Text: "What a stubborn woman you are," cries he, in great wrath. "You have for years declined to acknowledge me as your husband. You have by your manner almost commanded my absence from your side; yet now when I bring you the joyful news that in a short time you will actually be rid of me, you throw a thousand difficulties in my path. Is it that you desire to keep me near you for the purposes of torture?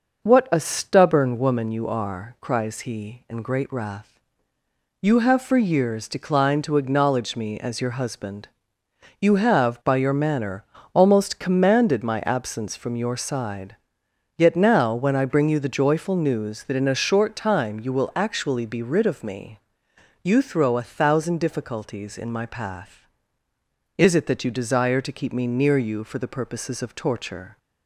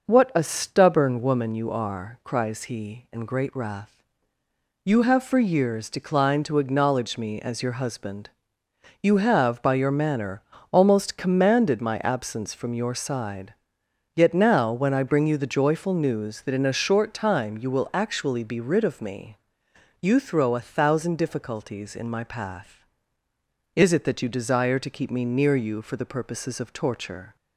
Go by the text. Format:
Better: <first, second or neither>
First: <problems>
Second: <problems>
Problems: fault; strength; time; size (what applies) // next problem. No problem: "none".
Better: neither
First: pauses between "manner" and "almost"; slight; at 10.6 s; 0.30 s long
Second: pauses between "manner" and "almost"; slight; at 10.4 s; 0.30 s long